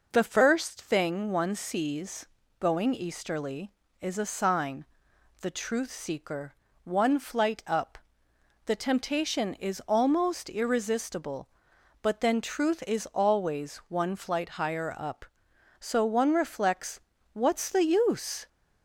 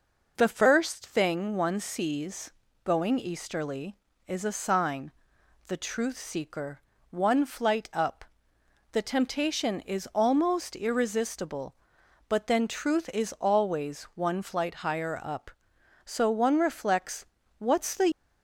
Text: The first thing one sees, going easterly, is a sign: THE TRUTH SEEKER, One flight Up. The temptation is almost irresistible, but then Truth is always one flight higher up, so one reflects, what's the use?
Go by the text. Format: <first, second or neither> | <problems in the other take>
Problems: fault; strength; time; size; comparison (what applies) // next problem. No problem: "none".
first | stops before "use"; at 18.1 s